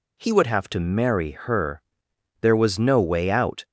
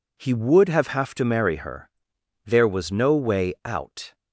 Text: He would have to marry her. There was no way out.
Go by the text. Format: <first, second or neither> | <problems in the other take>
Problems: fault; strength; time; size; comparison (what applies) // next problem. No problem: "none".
first | says "have" twice; at 0.8 s